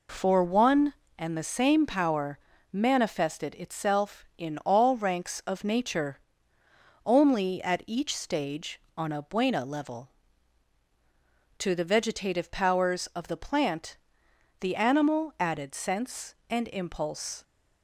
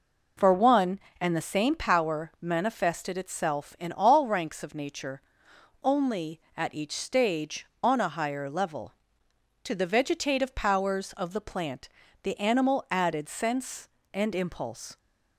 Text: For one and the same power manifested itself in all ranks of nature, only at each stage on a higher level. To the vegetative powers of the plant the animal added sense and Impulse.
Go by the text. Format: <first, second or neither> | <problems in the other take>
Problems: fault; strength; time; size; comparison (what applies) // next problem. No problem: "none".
second | pauses between "power" and "manifested"; slight; at 2.4 s; 0.32 s long // says "buena" for "higher"; at 9.2 s // pauses between "plant" and "the"; noticeable; at 13.9 s; 0.62 s long; slight in the second